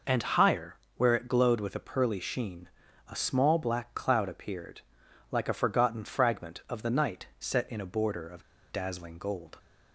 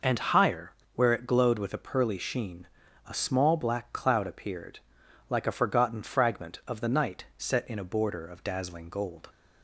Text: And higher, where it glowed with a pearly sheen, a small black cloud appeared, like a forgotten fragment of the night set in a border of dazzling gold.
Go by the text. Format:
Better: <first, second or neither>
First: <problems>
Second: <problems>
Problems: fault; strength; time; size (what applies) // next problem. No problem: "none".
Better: second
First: pauses between "of" and "dazzling"; slight; at 8.4 s; 0.29 s long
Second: none